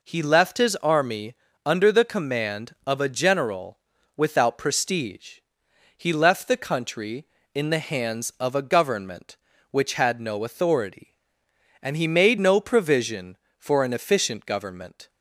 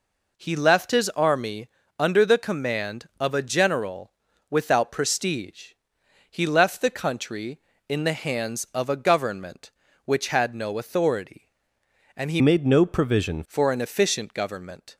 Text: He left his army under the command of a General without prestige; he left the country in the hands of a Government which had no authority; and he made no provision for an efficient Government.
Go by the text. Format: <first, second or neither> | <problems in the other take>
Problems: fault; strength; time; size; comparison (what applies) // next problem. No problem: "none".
first | pauses between "army" and "under"; slight; at 1.6 s; 0.30 s long; slight in the first // pauses between "General" and "without"; at 4.1 s; 0.40 s long; also in the first // changes voice from "made" to "provision"; from 12.4 to 13.4 s; 1.0 s long